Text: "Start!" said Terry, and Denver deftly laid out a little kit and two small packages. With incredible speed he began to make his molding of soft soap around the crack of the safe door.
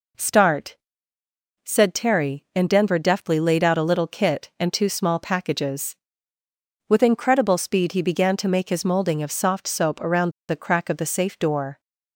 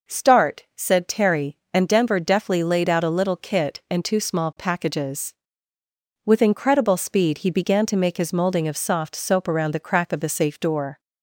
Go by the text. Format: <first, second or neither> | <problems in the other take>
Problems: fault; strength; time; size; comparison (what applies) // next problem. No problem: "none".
second | pauses between "around" and "the"; slight; at 10.2 s; 0.20 s long